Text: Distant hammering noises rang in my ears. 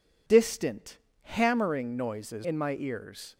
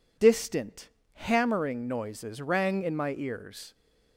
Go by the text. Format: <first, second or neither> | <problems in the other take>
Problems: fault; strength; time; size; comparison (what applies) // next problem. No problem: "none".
second | pauses between "Distant" and "hammering"; slight; at 0.9 s; 0.24 s long; slight in the second // skips "rang"; at 2.4 s